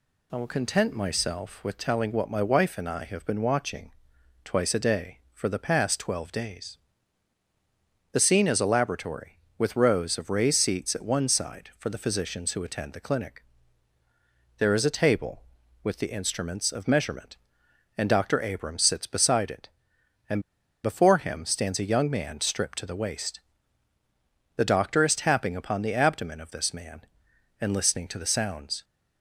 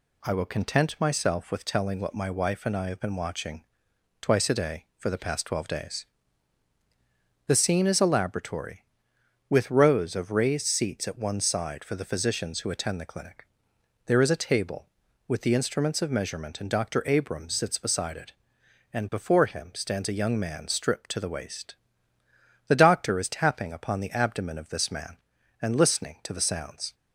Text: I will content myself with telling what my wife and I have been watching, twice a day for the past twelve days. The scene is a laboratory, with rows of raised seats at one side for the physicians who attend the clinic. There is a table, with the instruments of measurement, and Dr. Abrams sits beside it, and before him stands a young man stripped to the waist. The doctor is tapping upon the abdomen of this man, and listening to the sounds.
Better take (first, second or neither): second